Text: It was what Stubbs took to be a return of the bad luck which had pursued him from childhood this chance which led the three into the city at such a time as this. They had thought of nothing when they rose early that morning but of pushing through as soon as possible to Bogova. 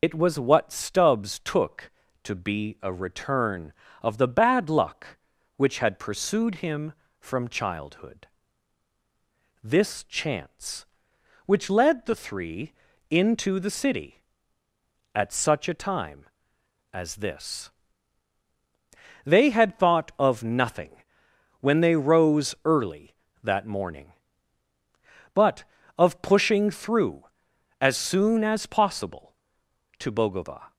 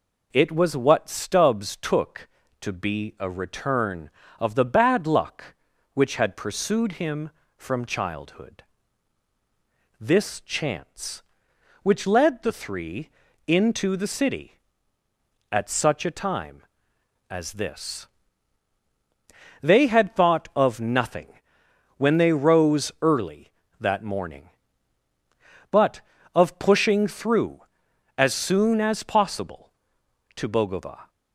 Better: second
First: loses the start of "It"; at 0.0 s; 80 ms // pauses between "childhood" and "this"; strong; at 8.2 s; 1.3 s long // pauses between "three" and "into"; at 12.7 s; 0.38 s long // pauses between "nothing" and "when"; noticeable; at 20.9 s; 0.70 s long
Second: pauses between "childhood" and "this"; strong; at 8.6 s; 1.3 s long // pauses between "three" and "into"; at 13.0 s; 0.38 s long // pauses between "nothing" and "when"; noticeable; at 21.2 s; 0.70 s long

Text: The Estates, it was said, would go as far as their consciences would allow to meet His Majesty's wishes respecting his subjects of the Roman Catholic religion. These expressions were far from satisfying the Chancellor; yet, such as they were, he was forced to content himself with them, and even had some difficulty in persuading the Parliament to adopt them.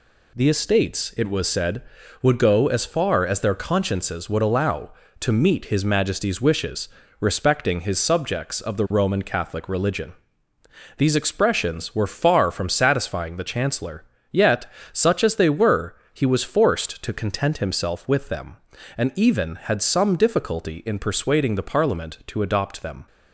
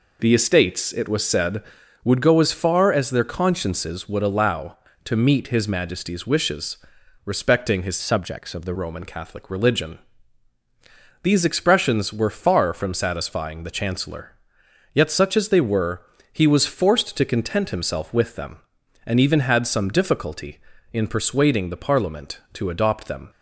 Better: first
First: pauses between "wishes" and "respecting"; slight; at 6.8 s; 0.30 s long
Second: pauses between "wishes" and "respecting"; noticeable; at 6.7 s; 0.50 s long // changes voice from "subjects" to "the"; from 8.0 to 8.7 s; 0.7 s long

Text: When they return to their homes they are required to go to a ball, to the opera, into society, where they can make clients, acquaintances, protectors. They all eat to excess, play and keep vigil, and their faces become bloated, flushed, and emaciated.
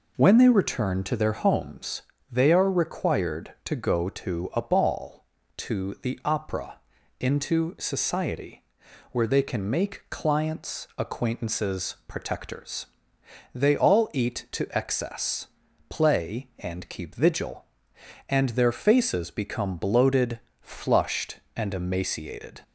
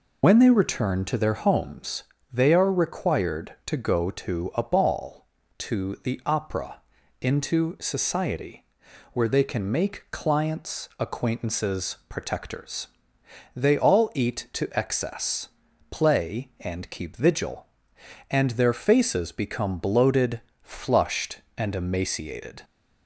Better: first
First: pauses between "homes" and "they"; slight; at 2.0 s; 0.30 s long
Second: loses the start of "When"; at 0.2 s; 55 ms // pauses between "homes" and "they"; slight; at 2.0 s; 0.30 s long

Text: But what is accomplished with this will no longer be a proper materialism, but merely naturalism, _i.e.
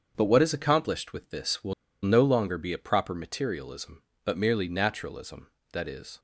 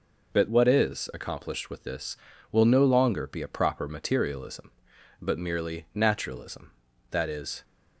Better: second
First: starts louder than the rest; until 1.1 s; 7 dB // pauses between "will" and "no"; slight; at 1.7 s; 0.29 s long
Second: none

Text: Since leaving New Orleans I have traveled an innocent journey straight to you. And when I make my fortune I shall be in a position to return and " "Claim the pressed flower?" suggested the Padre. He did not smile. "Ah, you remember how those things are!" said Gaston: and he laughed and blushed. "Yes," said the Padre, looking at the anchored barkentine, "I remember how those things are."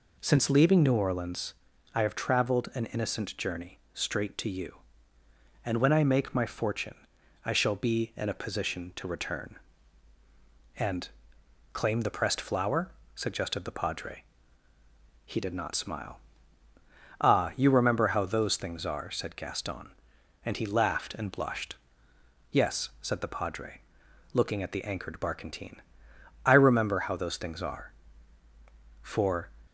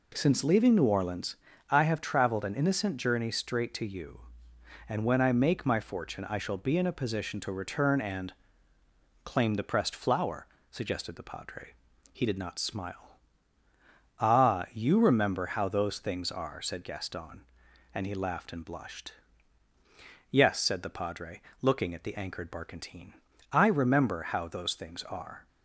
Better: second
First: pauses between "Orleans" and "I"; at 1.5 s; 0.40 s long // pauses between "journey" and "straight"; slight; at 3.7 s; 0.16 s long // pauses between "fortune" and "I"; noticeable; at 6.9 s; 0.48 s long // goes on to say "For"; from 29.0 s on; 0.50 s long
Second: pauses between "Orleans" and "I"; slight; at 1.3 s; 0.34 s long

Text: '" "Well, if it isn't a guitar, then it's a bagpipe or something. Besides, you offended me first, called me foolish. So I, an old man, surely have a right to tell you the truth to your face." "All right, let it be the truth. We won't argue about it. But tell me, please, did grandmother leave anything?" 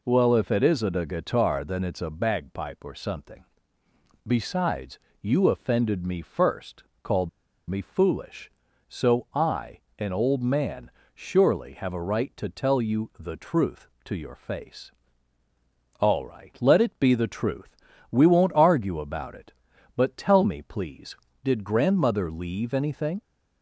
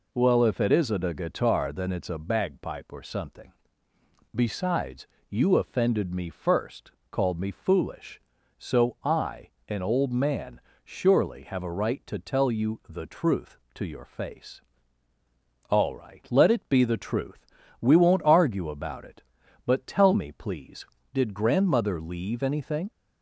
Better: second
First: pauses between "called" and "me"; at 7.2 s; 0.39 s long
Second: none

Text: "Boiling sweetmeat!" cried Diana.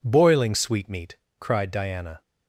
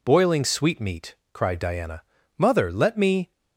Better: first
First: none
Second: goes on to say "Mother let me"; noticeable; from 2.3 s on; 0.94 s long

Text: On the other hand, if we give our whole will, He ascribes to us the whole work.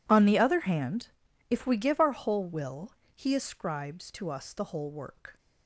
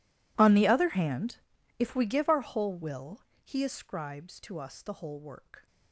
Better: first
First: none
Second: gets quieter; strong; throughout; 25 dB

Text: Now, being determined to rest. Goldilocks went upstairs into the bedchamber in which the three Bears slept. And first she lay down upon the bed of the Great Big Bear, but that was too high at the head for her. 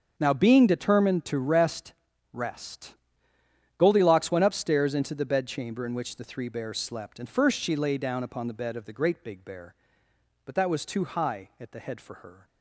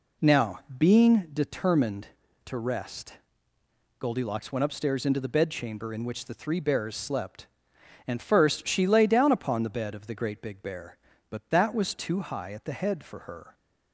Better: second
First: starts louder than the rest; strong; until 1.1 s; 7 dB // says "rest" twice; at 2.3 s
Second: none

